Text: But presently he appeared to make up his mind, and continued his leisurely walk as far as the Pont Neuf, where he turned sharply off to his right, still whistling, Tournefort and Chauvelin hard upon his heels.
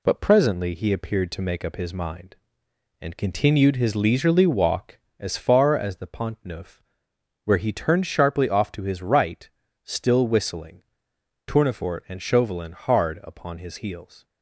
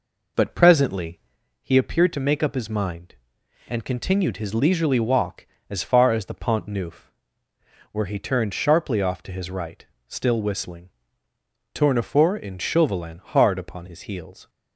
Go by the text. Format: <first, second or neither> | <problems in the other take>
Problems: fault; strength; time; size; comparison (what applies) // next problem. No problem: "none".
first | starts louder than the rest; noticeable; until 1.5 s; 4.5 dB // pauses between "presently" and "he"; at 1.1 s; 0.44 s long